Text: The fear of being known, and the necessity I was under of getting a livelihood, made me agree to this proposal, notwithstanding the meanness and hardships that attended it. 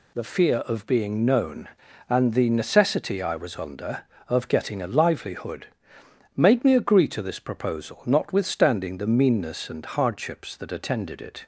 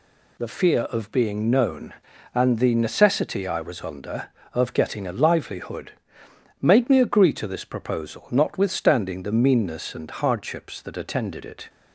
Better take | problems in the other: neither | none

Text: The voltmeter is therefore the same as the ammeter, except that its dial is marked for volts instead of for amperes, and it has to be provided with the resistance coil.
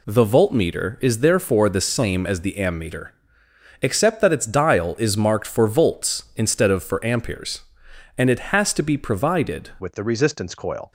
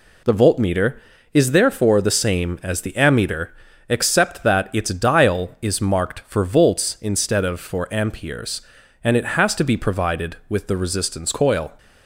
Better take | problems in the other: second | changes voice at "with"; from 9.7 s on; 1.2 s long

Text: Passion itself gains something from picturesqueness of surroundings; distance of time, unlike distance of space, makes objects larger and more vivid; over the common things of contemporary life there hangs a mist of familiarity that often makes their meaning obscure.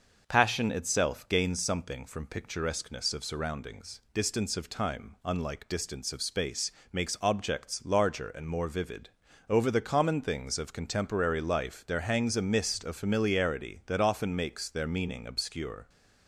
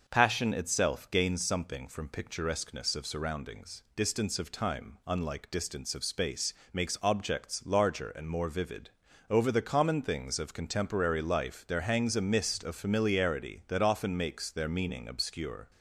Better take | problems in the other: neither | starts louder than the rest; noticeable; the same in both

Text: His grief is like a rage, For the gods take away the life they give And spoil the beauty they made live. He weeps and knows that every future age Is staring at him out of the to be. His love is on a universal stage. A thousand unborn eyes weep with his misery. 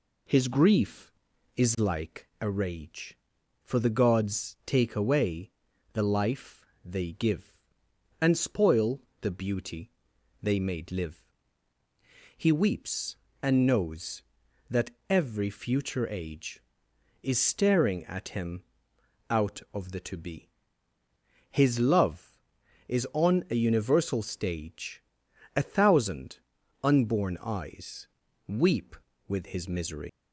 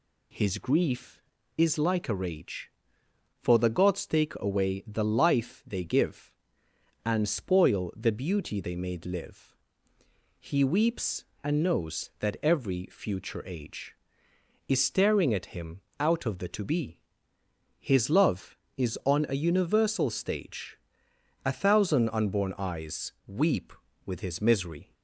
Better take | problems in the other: second | pauses between "away" and "the"; at 5.5 s; 0.42 s long // pauses between "life" and "they"; slight; at 6.6 s; 0.18 s long // pauses between "spoil" and "the"; slight; at 8.9 s; 0.22 s long // pauses between "beauty" and "they"; noticeable; at 9.8 s; 0.54 s long // pauses between "that" and "every"; slight; at 14.9 s; 0.18 s long // pauses between "him" and "out"; noticeable; at 18.6 s; 0.70 s long; slight in the second // pauses between "thousand" and "unborn"; noticeable; at 26.3 s; 0.46 s long // pauses between "eyes" and "weep"; at 28.0 s; 0.38 s long; slight in the second // leaves "misery" unfinished; at 30.0 s; 110 ms

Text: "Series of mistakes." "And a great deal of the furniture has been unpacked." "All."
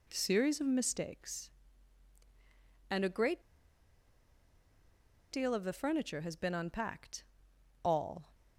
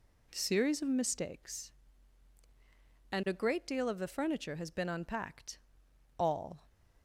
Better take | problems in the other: second | pauses between "great" and "deal"; strong; at 3.4 s; 1.9 s long

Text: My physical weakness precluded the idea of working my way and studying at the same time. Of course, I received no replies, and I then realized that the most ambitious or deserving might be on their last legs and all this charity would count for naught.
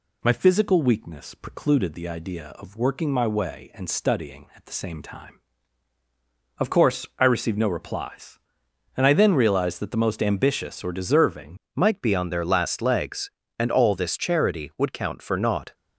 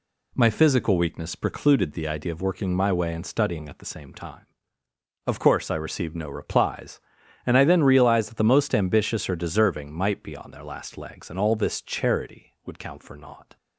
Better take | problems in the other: second | changes voice at "might"; from 11.7 s on; 4.0 s long

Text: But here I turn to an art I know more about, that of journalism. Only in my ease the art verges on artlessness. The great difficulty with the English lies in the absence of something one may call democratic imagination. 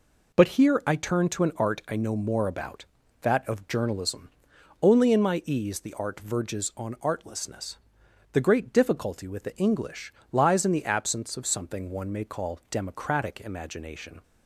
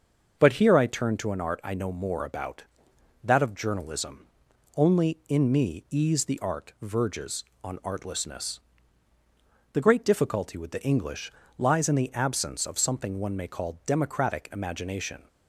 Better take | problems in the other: first | starts louder than the rest; until 1.4 s; 6.5 dB // says "me" for "my"; at 5.5 s // pauses between "English" and "lies"; slight; at 11.3 s; 0.26 s long; slight in the first

